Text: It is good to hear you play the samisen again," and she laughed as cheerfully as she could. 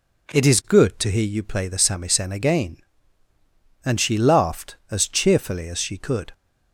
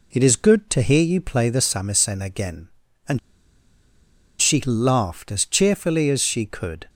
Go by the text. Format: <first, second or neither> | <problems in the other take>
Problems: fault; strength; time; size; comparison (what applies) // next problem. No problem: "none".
first | pauses between "and" and "she"; at 3.1 s; 1.2 s long